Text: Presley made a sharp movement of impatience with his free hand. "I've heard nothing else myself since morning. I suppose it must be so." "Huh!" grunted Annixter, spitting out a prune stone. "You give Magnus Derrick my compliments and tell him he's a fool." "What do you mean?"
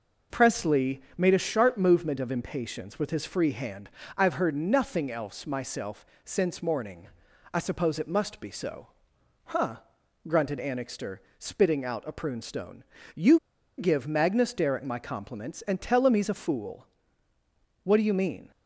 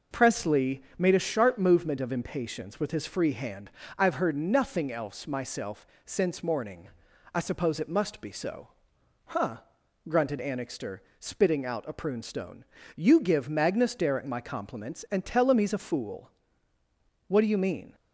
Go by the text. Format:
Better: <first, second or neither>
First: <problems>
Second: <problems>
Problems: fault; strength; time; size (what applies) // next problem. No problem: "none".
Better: second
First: pauses between "Presley" and "made"; slight; at 1.0 s; 0.16 s long // pauses between "myself" and "since"; slight; at 6.0 s; 0.18 s long // pauses between "You" and "give"; at 13.3 s; 0.39 s long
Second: pauses between "Presley" and "made"; slight; at 0.8 s; 0.16 s long // pauses between "myself" and "since"; slight; at 5.8 s; 0.18 s long